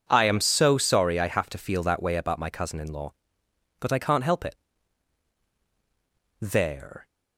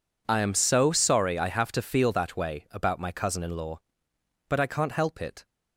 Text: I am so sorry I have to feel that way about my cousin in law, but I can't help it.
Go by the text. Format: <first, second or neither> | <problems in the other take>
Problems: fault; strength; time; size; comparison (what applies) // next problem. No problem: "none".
second | goes on to say "There"; noticeable; from 6.4 s on; 0.66 s long